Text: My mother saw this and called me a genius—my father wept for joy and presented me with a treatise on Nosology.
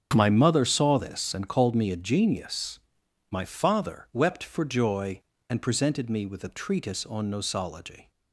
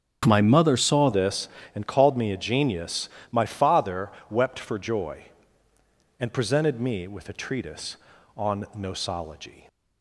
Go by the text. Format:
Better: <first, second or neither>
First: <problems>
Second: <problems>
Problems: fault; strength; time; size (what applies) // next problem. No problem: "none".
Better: first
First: starts louder than the rest; strong; until 1.1 s; 7 dB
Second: starts louder than the rest; strong; until 1.2 s; 8 dB // changes voice at "this"; from 1.1 s on; 8.5 s long // pauses between "father" and "wept"; slight; at 4.1 s; 0.20 s long